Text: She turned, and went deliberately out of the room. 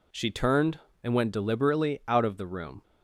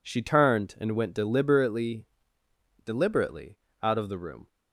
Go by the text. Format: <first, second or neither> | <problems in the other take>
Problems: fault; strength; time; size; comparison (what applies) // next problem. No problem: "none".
first | says "deliberately" twice; at 2.8 s